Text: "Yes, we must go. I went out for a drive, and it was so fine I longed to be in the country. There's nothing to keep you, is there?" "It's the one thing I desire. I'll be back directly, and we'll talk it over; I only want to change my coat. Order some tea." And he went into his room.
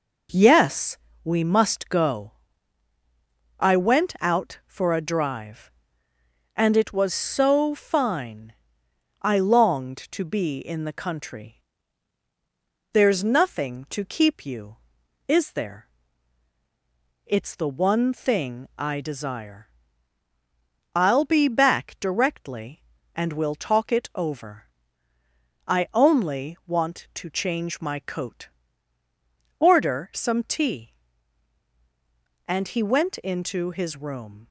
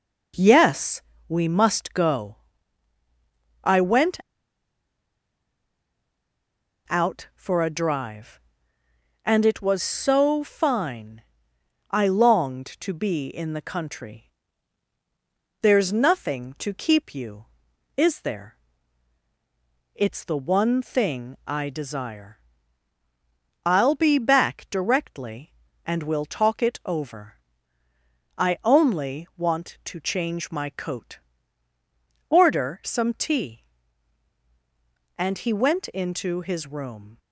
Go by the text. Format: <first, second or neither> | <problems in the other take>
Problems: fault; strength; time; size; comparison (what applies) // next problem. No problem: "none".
first | pauses between "went" and "out"; strong; at 4.1 s; 2.7 s long // pauses between "fine" and "I"; noticeable; at 11.2 s; 0.68 s long; noticeable in the first